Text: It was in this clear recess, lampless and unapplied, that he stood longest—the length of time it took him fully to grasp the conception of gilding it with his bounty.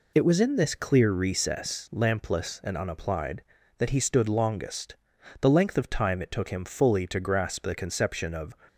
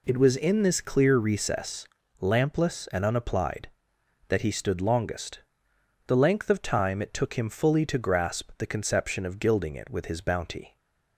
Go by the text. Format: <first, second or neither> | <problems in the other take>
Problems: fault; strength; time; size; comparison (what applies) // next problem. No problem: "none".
second | stops before "gilding it with his bounty"; at 8.6 s